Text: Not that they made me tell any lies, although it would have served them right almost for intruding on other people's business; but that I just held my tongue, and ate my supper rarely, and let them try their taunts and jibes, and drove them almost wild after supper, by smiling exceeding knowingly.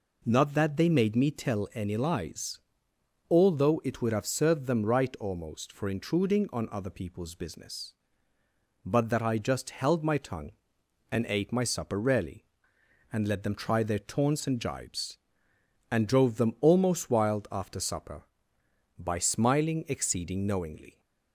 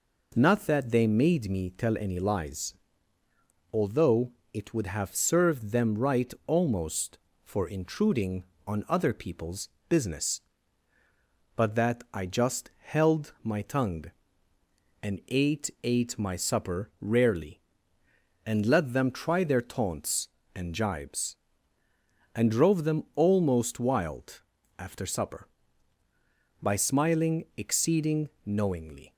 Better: first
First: none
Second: pauses between "although" and "it"; slight; at 4.3 s; 0.22 s long // pauses between "people's" and "business"; slight; at 9.6 s; 0.20 s long // says "ate" twice; at 15.8 s // pauses between "wild" and "after"; at 24.4 s; 0.38 s long // pauses between "exceeding" and "knowingly"; slight; at 28.2 s; 0.18 s long

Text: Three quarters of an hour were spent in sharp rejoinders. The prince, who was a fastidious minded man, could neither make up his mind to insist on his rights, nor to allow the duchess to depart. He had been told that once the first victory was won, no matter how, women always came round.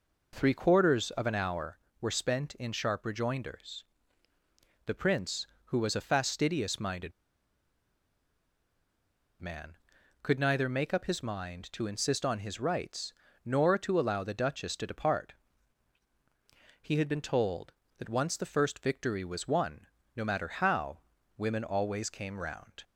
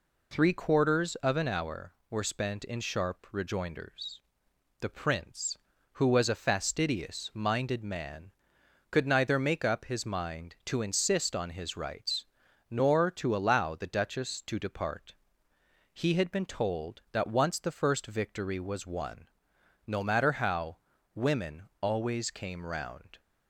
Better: second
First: pauses between "minded" and "man"; strong; at 7.1 s; 2.2 s long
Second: none

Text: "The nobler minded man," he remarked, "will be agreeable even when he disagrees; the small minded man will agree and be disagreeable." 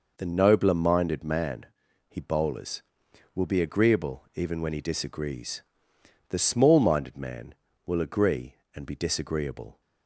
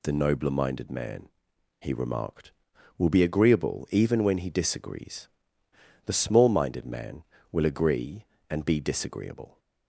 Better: second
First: says "bowlers" for "remarked"; at 2.2 s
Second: none

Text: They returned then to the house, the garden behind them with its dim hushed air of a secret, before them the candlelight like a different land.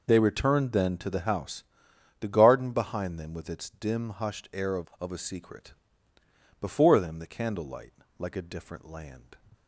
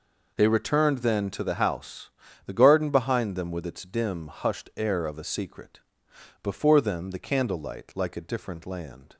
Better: second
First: says "of" twice; at 4.9 s // pauses between "candlelight" and "like"; slight; at 7.9 s; 0.28 s long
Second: none

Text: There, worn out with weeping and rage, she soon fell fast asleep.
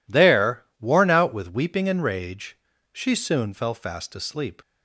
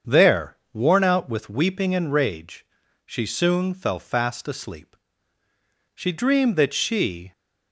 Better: first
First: none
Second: starts louder than the rest; until 1.2 s; 7 dB // goes on to say "She dreamed that she"; from 5.9 s on; 1.3 s long

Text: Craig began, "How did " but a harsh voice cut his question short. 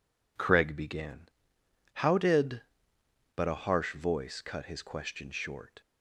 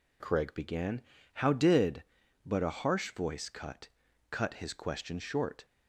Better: first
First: none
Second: says "cut" twice; at 4.2 s

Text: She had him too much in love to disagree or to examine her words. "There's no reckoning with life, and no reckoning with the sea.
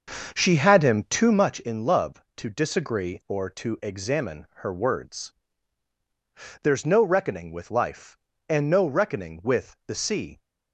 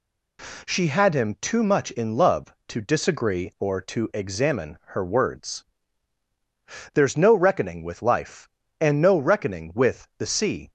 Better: second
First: starts louder than the rest; until 1.6 s; 6.5 dB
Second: none

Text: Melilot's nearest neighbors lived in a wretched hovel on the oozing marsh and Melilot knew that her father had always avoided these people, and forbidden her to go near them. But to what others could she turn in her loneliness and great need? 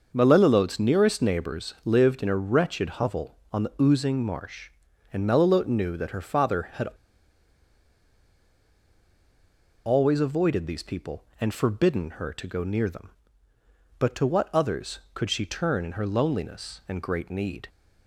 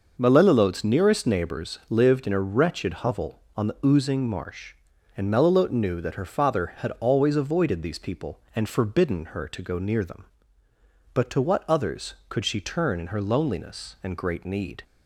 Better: second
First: pauses between "had" and "always"; strong; at 6.8 s; 2.9 s long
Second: none

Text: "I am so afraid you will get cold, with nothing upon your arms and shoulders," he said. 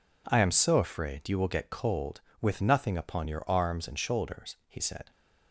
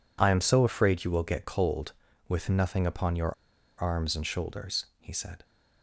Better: first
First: none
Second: pauses between "your" and "arms"; noticeable; at 3.3 s; 0.49 s long

